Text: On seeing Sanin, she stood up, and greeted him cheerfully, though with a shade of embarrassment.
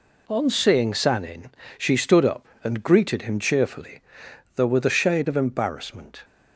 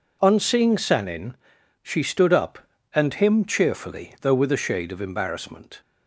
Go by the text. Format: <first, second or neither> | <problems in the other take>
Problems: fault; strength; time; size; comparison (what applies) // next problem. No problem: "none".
first | skips "greeted"; at 3.1 s